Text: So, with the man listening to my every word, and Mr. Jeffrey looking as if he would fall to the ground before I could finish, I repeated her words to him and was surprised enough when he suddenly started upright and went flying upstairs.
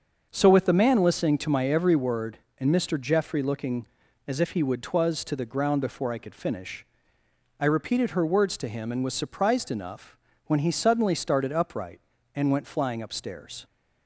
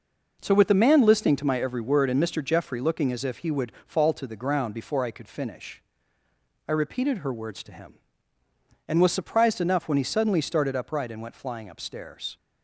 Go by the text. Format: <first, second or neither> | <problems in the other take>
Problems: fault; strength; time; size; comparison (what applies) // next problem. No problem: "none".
second | starts louder than the rest; until 1.3 s; 6.5 dB // says "twas" for "fall"; at 4.8 s // pauses between "enough" and "when"; slight; at 10.1 s; 0.28 s long